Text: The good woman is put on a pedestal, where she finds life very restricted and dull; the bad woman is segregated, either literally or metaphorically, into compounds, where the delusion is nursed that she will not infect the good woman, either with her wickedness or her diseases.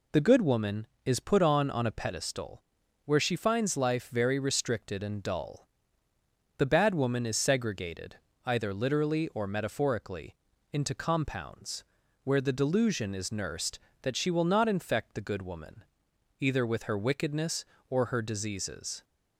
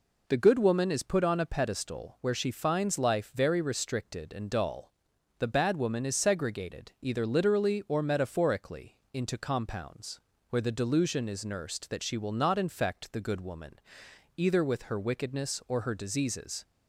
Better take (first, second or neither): second